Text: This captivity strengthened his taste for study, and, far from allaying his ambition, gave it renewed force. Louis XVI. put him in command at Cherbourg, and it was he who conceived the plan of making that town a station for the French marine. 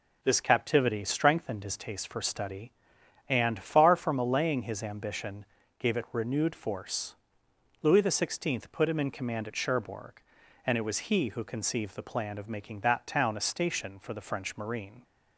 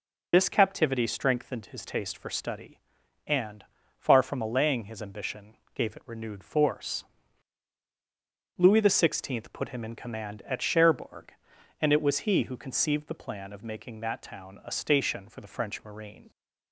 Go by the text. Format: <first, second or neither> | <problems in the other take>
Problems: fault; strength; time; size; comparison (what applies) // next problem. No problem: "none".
first | loses the start of "This"; at 0.3 s; 35 ms